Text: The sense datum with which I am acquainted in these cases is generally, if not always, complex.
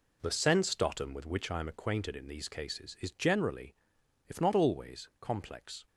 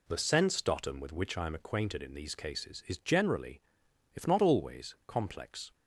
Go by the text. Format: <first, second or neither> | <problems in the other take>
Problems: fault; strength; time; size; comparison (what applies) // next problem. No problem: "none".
second | gets quieter; strong; throughout; 10.5 dB